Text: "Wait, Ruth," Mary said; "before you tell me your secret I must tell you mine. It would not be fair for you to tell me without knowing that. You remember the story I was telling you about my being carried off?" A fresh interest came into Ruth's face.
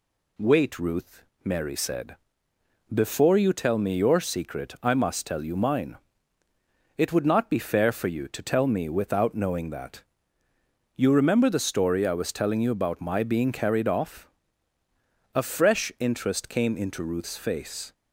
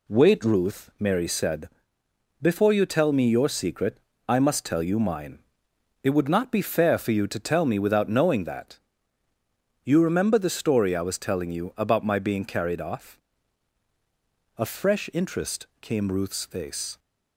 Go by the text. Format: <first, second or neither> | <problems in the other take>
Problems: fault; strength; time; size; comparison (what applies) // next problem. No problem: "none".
first | pauses between "secret" and "I"; slight; at 3.9 s; 0.28 s long // skips "into"; at 16.1 s